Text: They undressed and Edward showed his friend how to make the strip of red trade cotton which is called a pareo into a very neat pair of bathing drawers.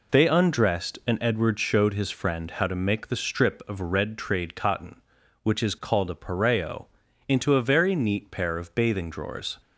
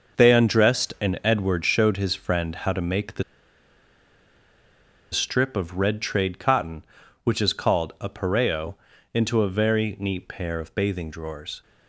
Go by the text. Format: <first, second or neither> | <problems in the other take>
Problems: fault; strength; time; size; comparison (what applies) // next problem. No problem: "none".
first | pauses between "the" and "strip"; strong; at 3.2 s; 1.9 s long // pauses between "pareo" and "into"; at 8.7 s; 0.40 s long; also in the first